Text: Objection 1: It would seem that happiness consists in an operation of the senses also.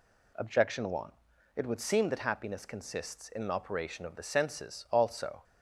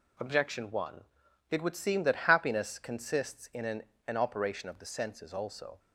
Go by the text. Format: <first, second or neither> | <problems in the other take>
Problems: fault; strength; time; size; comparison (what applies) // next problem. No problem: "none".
first | says "an" twice; at 4.0 s